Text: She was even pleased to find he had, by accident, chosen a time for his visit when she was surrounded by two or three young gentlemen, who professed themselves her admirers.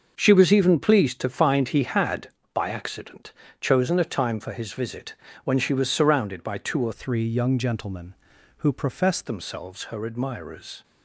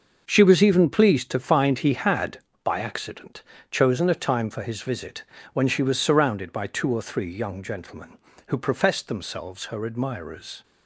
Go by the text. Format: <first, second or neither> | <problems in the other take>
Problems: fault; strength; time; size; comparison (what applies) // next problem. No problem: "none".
second | starts louder than the rest; noticeable; until 1.1 s; 6 dB // pauses between "visit" and "when"; slight; at 5.1 s; 0.30 s long; slight in the second // changes voice from "three" to "professed"; from 6.9 to 9.2 s; 2.3 s long